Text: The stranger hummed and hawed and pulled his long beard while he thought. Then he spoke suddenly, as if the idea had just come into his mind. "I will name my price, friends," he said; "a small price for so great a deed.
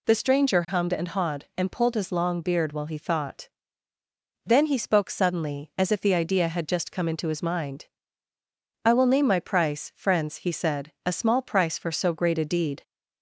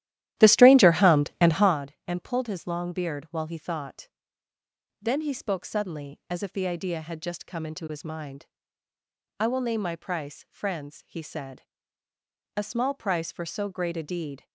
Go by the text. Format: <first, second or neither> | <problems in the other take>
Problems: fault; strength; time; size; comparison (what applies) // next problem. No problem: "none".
first | starts louder than the rest; strong; until 1.8 s; 13 dB